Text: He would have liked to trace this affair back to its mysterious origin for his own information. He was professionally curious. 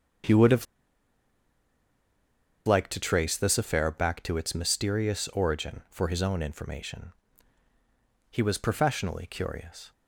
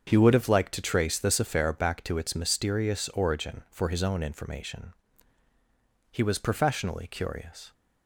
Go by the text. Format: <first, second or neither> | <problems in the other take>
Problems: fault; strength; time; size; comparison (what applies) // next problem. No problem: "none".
second | starts louder than the rest; until 3.2 s; 7 dB; also in the second // pauses between "have" and "liked"; strong; at 0.6 s; 2.0 s long